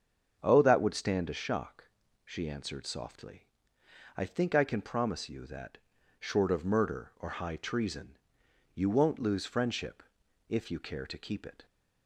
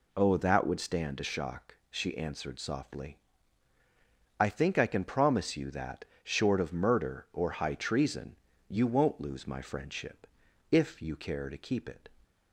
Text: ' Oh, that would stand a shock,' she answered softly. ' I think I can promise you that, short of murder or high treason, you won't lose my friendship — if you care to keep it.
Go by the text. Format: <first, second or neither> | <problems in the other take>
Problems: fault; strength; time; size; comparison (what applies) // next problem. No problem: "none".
second | starts louder than the rest; until 1.3 s; 7 dB // skips "my"; at 9.4 s